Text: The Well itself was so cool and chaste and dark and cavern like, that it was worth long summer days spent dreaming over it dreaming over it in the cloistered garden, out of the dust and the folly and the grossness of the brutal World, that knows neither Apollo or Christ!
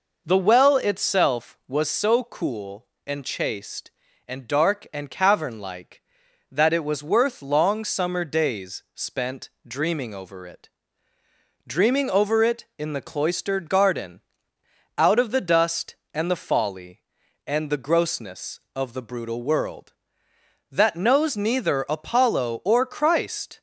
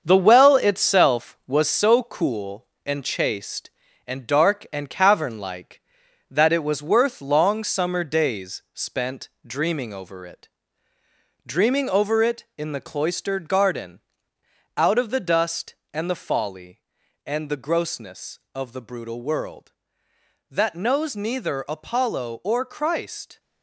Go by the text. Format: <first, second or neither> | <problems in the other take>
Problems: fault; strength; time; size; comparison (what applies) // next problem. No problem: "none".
first | gets quieter; throughout; 6.5 dB // pauses between "spent" and "dreaming"; slight; at 9.2 s; 0.18 s long; slight in the first // pauses between "it" and "dreaming"; noticeable; at 10.4 s; 0.98 s long; noticeable in the first